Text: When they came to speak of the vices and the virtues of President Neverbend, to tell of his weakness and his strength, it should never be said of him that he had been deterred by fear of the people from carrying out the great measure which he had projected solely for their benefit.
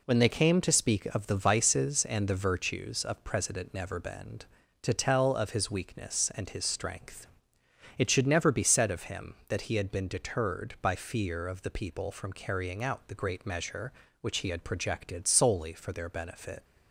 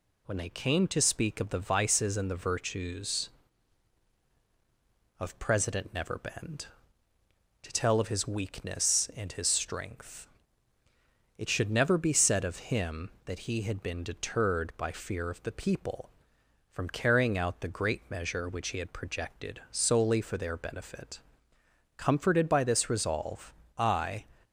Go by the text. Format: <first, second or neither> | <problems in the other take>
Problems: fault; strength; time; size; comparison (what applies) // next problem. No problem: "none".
first | goes on to say "Comforted by this resolve I"; strong; from 21.9 s on; 2.2 s long